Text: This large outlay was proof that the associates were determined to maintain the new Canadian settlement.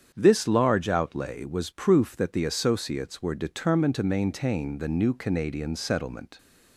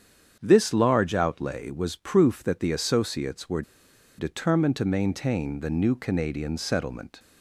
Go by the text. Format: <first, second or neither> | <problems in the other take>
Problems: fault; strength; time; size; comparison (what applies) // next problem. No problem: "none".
first | starts louder than the rest; strong; until 1.4 s; 8 dB; strong in the first // pauses between "were" and "determined"; noticeable; at 3.6 s; 0.56 s long